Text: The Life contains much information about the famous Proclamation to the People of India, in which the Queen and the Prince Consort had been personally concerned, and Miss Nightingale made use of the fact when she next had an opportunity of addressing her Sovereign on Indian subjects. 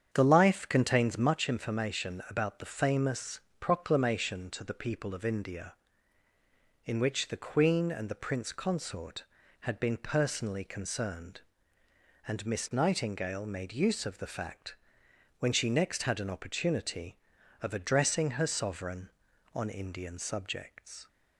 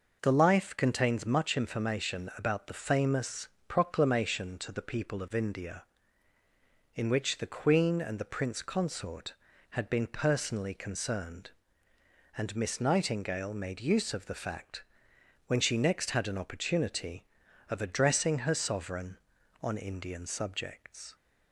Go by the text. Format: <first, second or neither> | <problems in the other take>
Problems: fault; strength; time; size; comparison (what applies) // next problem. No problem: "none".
second | starts louder than the rest; strong; until 1.3 s; 8 dB // pauses between "famous" and "Proclamation"; slight; at 3.3 s; 0.22 s long; slight in the second // pauses between "fact" and "when"; noticeable; at 14.7 s; 0.64 s long; noticeable in the second